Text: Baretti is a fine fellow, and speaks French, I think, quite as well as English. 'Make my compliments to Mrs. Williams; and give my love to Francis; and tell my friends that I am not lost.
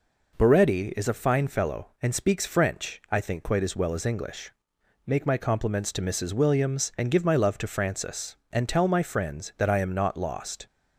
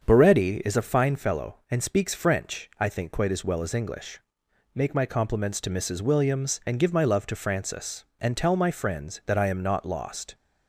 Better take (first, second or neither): first